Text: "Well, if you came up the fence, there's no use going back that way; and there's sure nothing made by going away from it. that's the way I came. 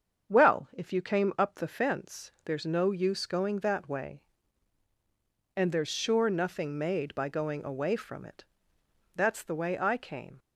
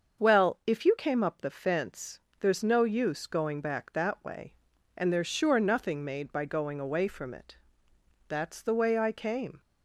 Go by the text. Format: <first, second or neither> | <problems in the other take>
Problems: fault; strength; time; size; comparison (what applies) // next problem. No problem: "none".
second | starts louder than the rest; strong; until 1.3 s; 7 dB; also in the second // skips "back"; at 3.5 s